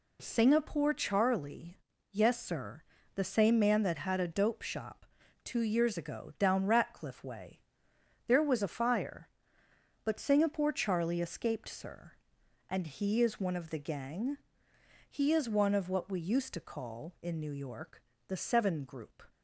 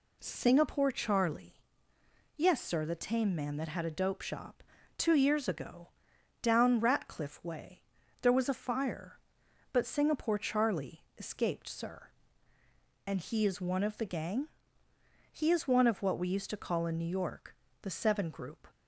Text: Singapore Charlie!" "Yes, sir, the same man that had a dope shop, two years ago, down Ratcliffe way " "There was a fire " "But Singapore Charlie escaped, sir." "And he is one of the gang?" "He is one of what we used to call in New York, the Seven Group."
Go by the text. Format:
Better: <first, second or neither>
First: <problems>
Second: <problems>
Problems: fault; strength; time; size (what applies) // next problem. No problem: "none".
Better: first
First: none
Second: says "tame" for "same"; at 2.9 s